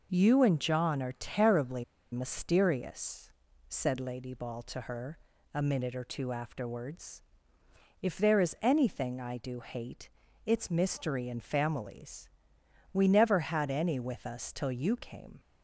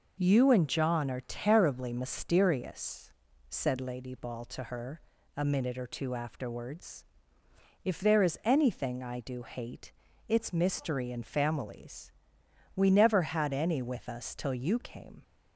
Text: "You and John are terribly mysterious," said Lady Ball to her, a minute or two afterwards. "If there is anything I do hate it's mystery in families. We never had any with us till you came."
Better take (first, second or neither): second